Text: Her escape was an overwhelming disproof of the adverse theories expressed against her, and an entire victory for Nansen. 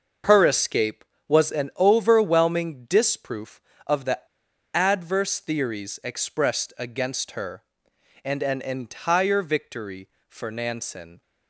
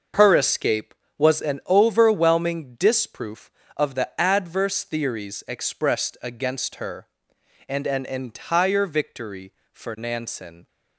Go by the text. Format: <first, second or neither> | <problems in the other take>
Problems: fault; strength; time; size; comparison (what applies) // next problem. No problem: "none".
second | pauses between "the" and "adverse"; noticeable; at 4.1 s; 0.55 s long